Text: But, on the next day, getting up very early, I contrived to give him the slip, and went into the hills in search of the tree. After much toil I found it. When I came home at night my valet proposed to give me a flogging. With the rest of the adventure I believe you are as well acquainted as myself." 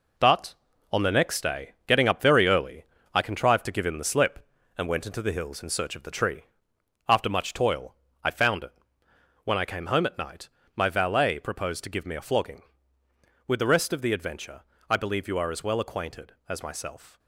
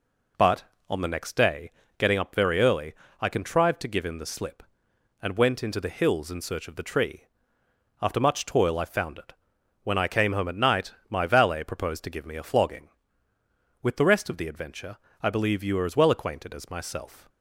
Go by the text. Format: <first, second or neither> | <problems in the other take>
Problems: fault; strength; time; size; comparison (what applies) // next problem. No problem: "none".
second | gets quieter; throughout; 7 dB // pauses between "toil" and "I"; slight; at 7.9 s; 0.28 s long // pauses between "night" and "my"; slight; at 10.4 s; 0.26 s long; slight in the second // pauses between "adventure" and "I"; slight; at 14.6 s; 0.30 s long; slight in the second